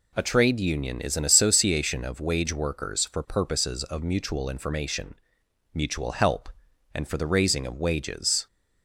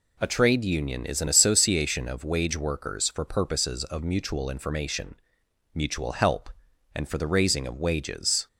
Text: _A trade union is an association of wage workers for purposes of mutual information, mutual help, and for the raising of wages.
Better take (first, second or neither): neither